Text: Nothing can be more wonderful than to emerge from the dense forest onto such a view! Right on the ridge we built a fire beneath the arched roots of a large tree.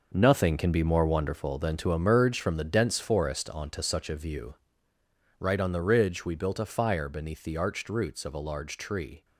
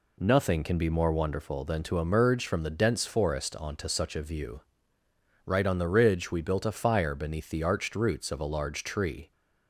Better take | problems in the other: second | gets quieter; strong; throughout; 9.5 dB

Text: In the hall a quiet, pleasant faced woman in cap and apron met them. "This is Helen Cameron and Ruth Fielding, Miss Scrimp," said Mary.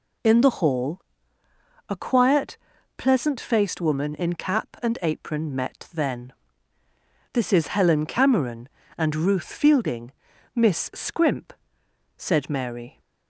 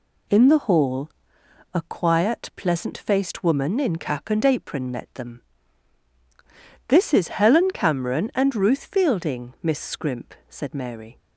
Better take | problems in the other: second | pauses between "hall" and "a"; noticeable; at 0.9 s; 0.88 s long; noticeable in the second // says "then" for "them"; at 5.9 s

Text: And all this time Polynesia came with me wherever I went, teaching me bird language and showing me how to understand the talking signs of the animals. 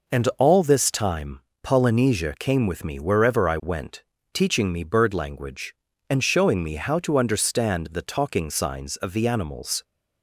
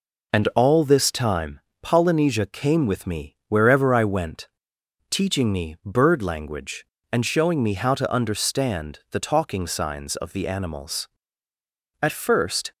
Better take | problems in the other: first | pauses between "time" and "Polynesia"; slight; at 1.5 s; 0.22 s long; slight in the first // goes on to say "At first"; noticeable; from 12.0 s on; 0.70 s long

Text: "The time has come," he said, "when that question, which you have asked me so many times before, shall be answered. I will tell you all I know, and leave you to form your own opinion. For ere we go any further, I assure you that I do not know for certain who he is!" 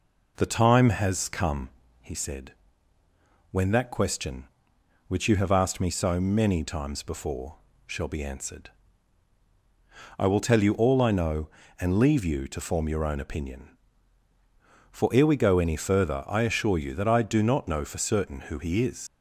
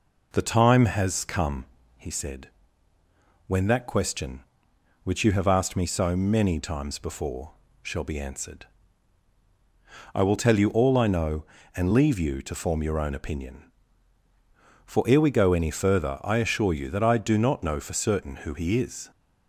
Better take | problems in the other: second | leaves "is" unfinished; at 19.0 s; 80 ms

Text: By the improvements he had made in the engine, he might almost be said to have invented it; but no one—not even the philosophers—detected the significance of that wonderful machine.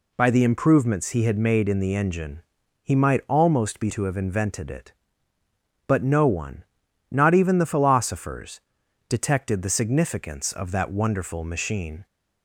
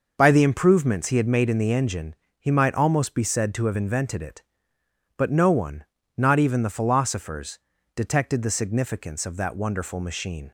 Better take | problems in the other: second | skips "said"; at 3.9 s

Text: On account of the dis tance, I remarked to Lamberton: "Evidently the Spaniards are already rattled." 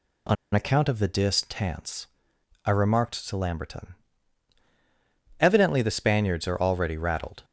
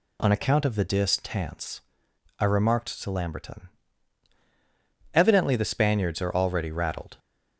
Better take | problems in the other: second | pauses between "On" and "account"; slight; at 0.3 s; 0.18 s long

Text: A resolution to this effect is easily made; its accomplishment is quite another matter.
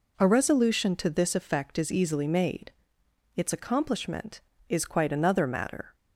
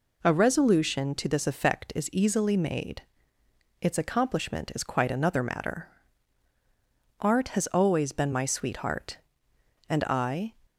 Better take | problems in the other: first | goes on to say "Art has always been my sweetheart and I"; strong; from 7.1 s on; 3.3 s long

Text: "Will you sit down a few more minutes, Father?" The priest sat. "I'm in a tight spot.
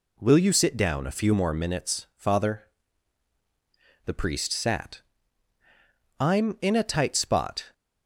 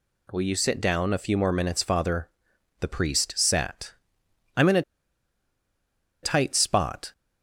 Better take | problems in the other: first | pauses between "a" and "tight"; strong; at 4.8 s; 1.4 s long

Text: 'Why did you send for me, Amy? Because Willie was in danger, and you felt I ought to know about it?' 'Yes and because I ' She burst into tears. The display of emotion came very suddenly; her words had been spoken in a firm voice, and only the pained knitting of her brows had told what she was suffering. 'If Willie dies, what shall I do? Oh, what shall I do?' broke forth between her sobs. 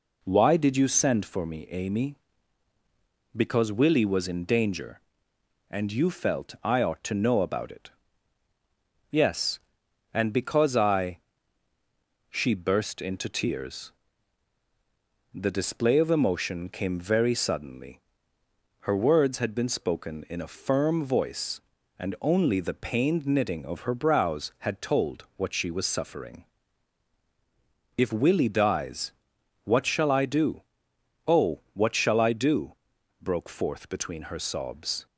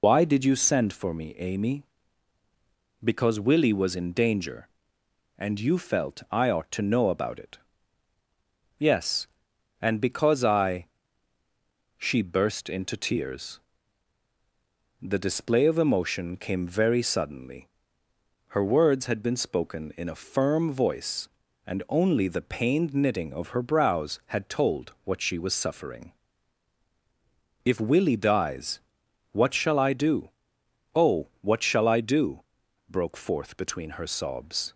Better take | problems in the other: first | loses the start of "Why"; at 0.0 s; 125 ms

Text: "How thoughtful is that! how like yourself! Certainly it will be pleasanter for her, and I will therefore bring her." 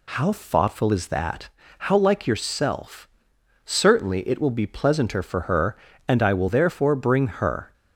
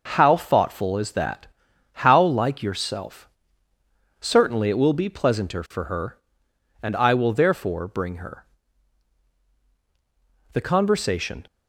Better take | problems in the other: first | goes on to say "The conversation"; noticeable; from 10.5 s on; 0.94 s long

